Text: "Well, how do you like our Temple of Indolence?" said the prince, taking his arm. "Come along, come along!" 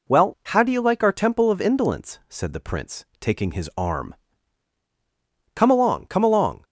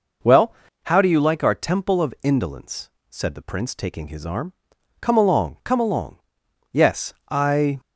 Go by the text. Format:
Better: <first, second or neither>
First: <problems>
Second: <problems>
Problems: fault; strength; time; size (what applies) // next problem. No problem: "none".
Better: first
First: none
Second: goes on to say "Yes I"; noticeable; from 6.7 s on; 1.0 s long